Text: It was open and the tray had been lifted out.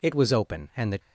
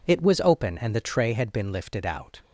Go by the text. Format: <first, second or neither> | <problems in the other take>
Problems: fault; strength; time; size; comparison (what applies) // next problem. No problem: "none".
second | stops before "tray had been lifted out"; at 0.9 s